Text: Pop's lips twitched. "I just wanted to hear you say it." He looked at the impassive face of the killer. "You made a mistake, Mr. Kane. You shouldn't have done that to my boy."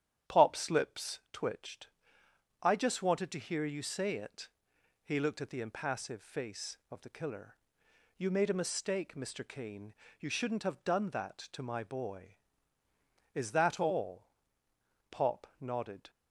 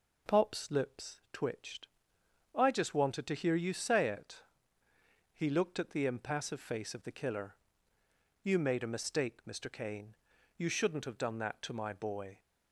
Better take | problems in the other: second | starts louder than the rest; strong; until 1.4 s; 10 dB // goes on to say "Is that all Pop nodded"; strong; from 13.3 s on; 2.7 s long

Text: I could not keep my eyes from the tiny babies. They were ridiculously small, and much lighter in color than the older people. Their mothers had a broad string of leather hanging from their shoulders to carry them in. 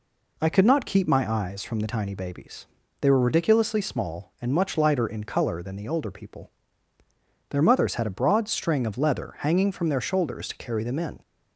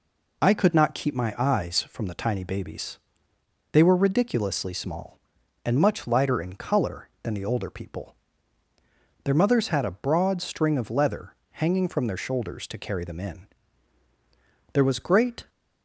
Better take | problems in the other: first | pauses between "leather" and "hanging"; slight; at 11.3 s; 0.18 s long // goes on to say "There was great"; noticeable; from 14.7 s on; 0.76 s long

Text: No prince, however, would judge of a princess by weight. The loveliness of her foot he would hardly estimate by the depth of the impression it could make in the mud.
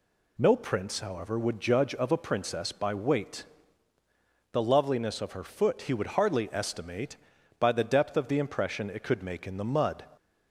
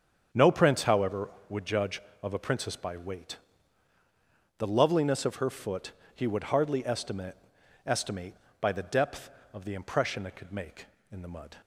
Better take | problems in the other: first | starts louder than the rest; strong; until 1.5 s; 7.5 dB // pauses between "foot" and "he"; slight; at 5.9 s; 0.22 s long // says "estimate" twice; at 7.8 s

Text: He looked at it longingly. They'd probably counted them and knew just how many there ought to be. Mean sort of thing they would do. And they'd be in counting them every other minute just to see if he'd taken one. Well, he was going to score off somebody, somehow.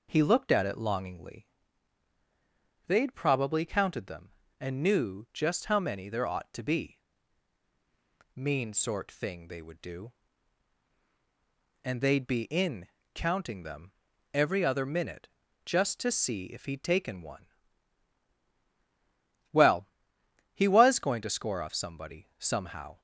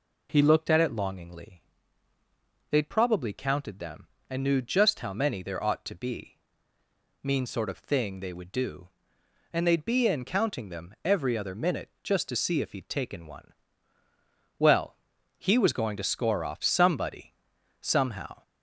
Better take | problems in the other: second | skips "of"; at 9.1 s // pauses between "in" and "counting"; slight; at 12.8 s; 0.26 s long // pauses between "them" and "every"; at 13.9 s; 0.42 s long // pauses between "minute" and "just"; slight; at 15.2 s; 0.36 s long; slight in the second

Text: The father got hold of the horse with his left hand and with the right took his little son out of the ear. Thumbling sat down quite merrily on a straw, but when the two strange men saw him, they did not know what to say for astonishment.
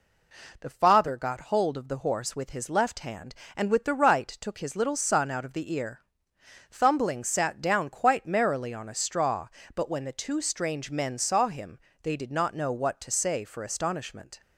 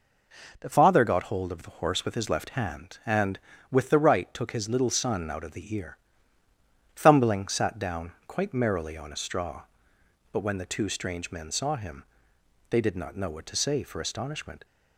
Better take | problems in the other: first | changes voice at "father"; from 0.7 s on; 13.9 s long // pauses between "down" and "quite"; slight; at 8.1 s; 0.16 s long

